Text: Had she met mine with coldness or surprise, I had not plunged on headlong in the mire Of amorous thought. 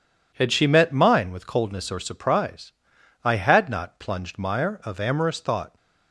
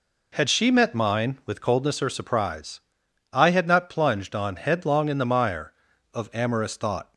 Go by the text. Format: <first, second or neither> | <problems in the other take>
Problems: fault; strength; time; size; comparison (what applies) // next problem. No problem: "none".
second | skips "on headlong in the"; at 4.3 s